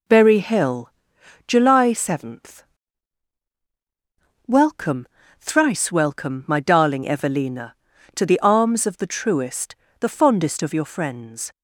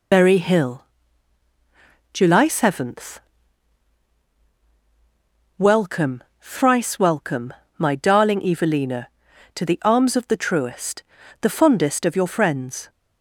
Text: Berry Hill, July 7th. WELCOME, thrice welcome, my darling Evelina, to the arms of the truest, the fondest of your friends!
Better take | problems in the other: first | loses the start of "Berry"; at 0.1 s; 50 ms

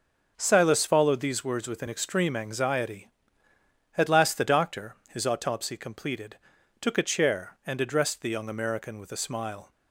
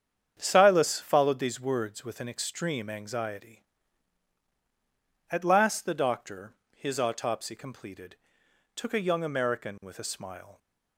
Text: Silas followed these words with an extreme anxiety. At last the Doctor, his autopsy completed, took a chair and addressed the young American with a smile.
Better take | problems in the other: first | starts louder than the rest; strong; until 1.3 s; 8 dB; also in the first // skips "chair and addressed the"; at 8.9 s

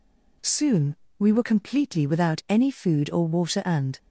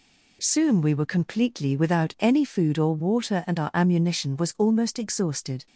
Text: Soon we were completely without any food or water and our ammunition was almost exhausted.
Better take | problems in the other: second | pauses between "Soon" and "we"; slight; at 0.9 s; 0.24 s long // stops before "our ammunition was almost exhausted"; at 3.9 s

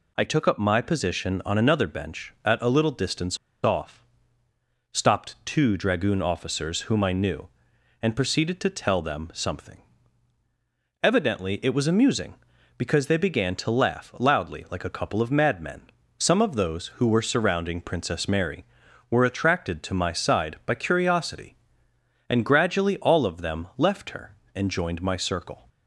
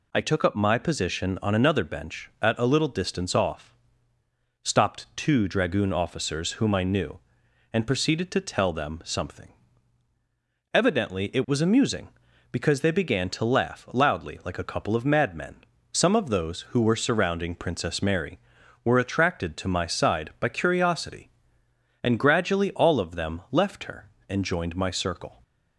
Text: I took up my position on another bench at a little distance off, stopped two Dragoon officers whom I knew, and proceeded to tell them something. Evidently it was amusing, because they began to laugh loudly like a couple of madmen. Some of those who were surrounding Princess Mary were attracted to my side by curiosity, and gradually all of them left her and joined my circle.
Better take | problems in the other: second | pauses between "distance" and "off"; slight; at 3.3 s; 0.27 s long

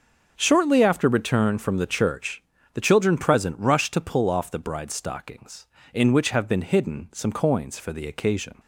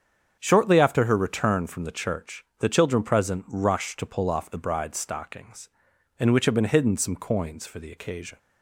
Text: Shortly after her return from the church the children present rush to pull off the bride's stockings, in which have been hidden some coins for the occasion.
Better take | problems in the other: second | starts louder than the rest; until 1.3 s; 6 dB; strong in the second // skips "her"; at 1.0 s // pauses between "church" and "the"; slight; at 2.4 s; 0.32 s long; slight in the second

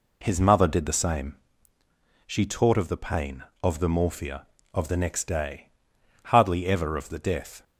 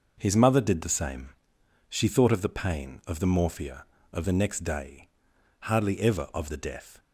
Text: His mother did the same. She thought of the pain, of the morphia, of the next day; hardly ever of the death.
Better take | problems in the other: second | says "taught" for "thought"; at 2.4 s

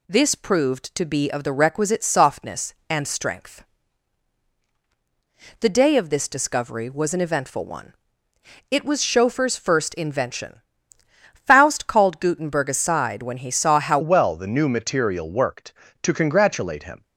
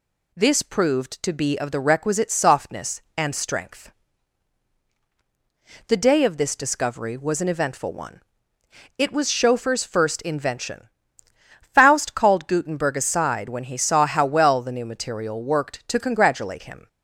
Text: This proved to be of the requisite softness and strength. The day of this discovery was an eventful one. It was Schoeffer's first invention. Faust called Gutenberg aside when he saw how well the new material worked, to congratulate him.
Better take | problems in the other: second | changes voice at "well"; from 14.0 s on; 3.0 s long

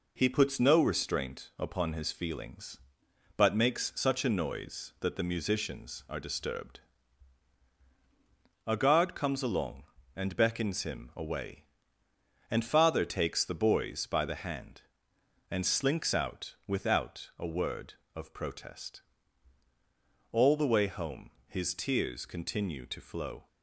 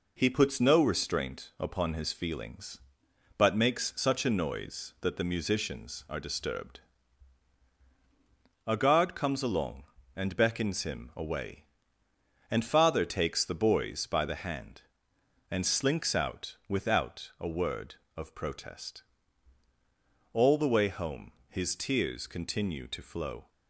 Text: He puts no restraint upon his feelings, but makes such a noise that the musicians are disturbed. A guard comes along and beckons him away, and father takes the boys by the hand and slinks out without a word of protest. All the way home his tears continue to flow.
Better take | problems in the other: neither | pauses between "home" and "his"; slight; the same in both

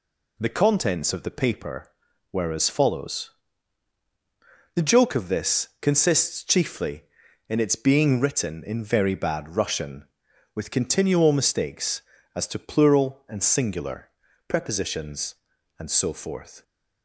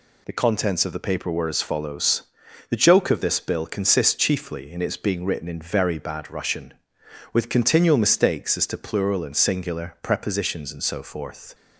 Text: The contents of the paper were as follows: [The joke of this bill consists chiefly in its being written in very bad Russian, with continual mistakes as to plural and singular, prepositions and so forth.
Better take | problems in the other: second | skips "bill"; at 5.7 s

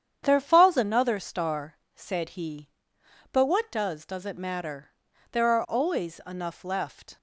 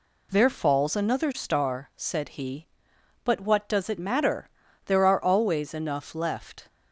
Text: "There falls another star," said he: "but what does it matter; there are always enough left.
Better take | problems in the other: second | starts louder than the rest; strong; until 1.2 s; 8.5 dB // says "does" twice; at 4.0 s

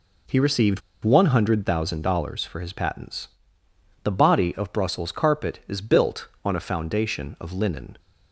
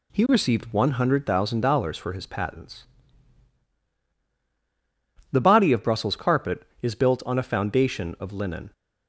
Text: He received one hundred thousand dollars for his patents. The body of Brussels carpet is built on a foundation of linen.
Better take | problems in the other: second | pauses between "received" and "one"; slight; at 0.8 s; 0.23 s long

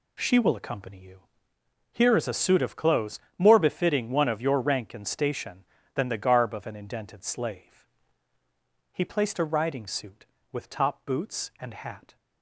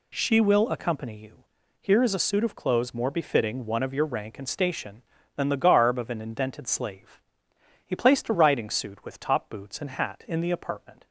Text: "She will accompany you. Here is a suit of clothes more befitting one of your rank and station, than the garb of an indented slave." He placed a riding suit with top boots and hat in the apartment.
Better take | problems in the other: second | pauses between "clothes" and "more"; slight; at 3.2 s; 0.18 s long // stops before "in the apartment"; at 12.1 s

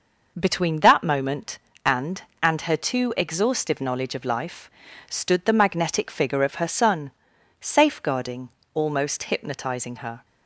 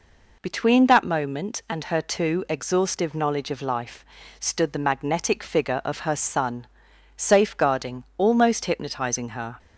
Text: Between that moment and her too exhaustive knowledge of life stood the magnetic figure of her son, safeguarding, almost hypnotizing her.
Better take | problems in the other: second | says "and" twice; at 2.4 s // pauses between "life" and "stood"; at 4.6 s; 0.40 s long; slight in the second

